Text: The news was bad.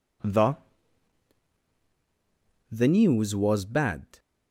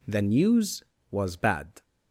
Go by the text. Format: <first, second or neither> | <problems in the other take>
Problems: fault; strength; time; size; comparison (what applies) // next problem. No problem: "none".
second | says "The" twice; at 2.6 s